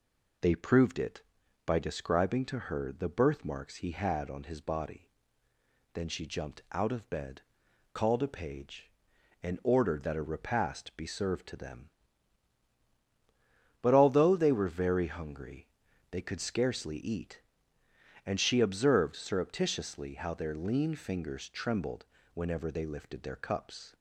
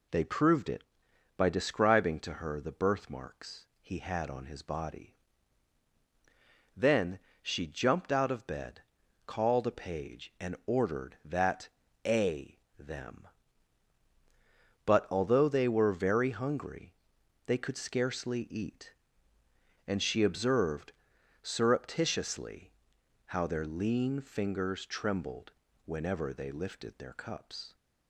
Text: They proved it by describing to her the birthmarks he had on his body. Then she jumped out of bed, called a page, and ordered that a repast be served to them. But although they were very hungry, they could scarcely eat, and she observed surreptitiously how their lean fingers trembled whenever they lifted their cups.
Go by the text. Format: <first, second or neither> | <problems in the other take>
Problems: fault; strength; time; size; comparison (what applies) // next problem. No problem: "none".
first | pauses between "Then" and "she"; slight; at 7.1 s; 0.24 s long // pauses between "that" and "a"; at 11.6 s; 0.38 s long // skips "repast be served to"; at 12.6 s // pauses between "observed" and "surreptitiously"; noticeable; at 20.9 s; 0.50 s long // pauses between "surreptitiously" and "how"; noticeable; at 22.7 s; 0.56 s long // pauses between "trembled" and "whenever"; slight; at 25.5 s; 0.34 s long; slight in the first